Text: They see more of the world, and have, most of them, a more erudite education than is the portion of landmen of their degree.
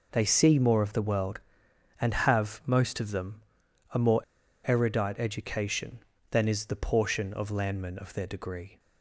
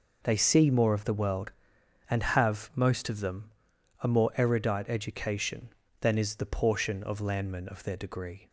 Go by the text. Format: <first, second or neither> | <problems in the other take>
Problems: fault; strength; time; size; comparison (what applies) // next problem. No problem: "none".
second | pauses between "more" and "erudite"; at 4.2 s; 0.45 s long